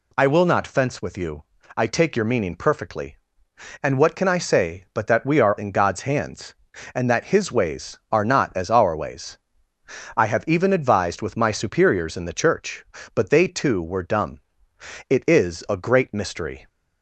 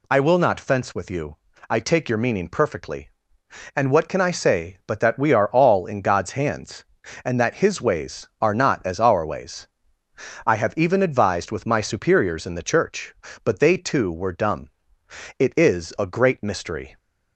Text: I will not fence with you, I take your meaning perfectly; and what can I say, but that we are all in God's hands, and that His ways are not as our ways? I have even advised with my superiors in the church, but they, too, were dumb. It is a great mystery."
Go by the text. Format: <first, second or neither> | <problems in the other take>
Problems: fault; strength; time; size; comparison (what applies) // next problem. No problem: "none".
second | skips "all"; at 5.5 s